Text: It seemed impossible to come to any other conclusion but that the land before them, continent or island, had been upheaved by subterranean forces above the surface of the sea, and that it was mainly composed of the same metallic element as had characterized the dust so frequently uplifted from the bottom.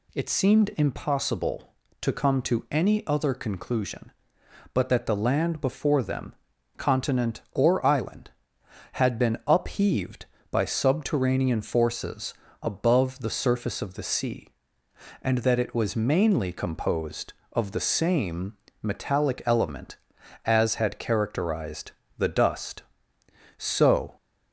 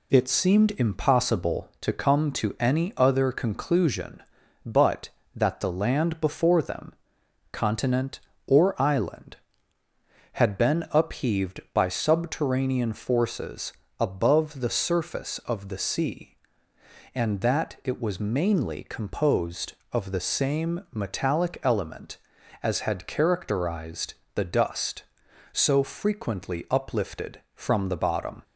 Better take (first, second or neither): second